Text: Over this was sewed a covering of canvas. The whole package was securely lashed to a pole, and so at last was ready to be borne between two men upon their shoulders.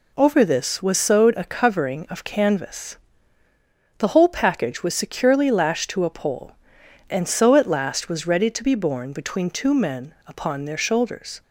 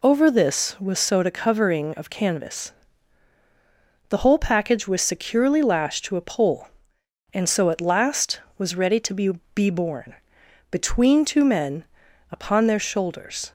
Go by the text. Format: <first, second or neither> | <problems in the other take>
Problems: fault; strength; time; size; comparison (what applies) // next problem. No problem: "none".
first | says "be" twice; at 9.5 s // pauses between "borne" and "between"; noticeable; at 10.1 s; 0.56 s long // pauses between "men" and "upon"; noticeable; at 11.8 s; 0.46 s long